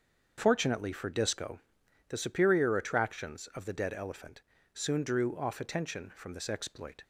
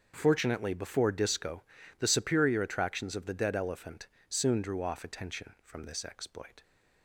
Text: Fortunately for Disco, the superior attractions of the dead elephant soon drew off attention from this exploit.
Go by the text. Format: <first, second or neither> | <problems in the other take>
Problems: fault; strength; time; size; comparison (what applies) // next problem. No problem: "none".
first | starts louder than the rest; until 1.1 s; 6.5 dB; also in the first // says "before" for "for"; at 0.7 s // pauses between "elephant" and "soon"; slight; at 4.0 s; 0.22 s long; slight in the first